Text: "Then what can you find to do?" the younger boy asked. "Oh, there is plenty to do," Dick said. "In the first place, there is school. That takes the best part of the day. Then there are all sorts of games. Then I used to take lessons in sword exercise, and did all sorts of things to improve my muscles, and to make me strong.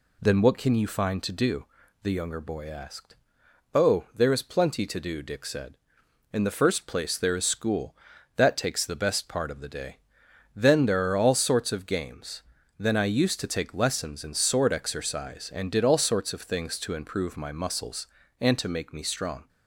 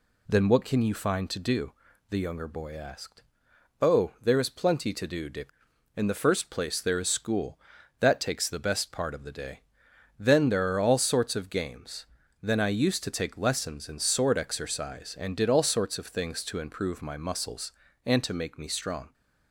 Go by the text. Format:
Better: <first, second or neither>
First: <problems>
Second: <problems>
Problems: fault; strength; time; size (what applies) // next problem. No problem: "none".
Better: first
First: none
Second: skips "said"; at 5.7 s